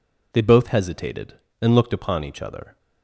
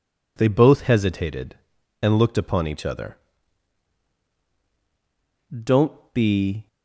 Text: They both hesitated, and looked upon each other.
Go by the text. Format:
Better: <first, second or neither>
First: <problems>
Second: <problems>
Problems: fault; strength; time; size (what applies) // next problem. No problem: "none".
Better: first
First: none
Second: goes on to say "Don't be"; noticeable; from 5.6 s on; 1.0 s long